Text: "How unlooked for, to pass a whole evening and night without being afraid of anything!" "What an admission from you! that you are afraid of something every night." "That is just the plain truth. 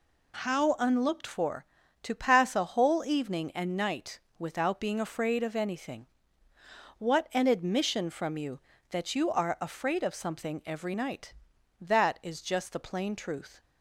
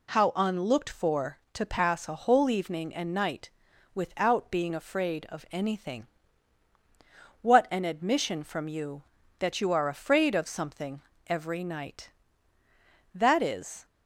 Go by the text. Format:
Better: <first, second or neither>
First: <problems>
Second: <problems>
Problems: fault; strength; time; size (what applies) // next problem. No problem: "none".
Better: first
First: pauses between "night" and "without"; slight; at 4.1 s; 0.18 s long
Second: pauses between "night" and "without"; at 3.5 s; 0.42 s long // pauses between "something" and "every"; slight; at 11.0 s; 0.24 s long // stops before "just the plain truth"; at 13.8 s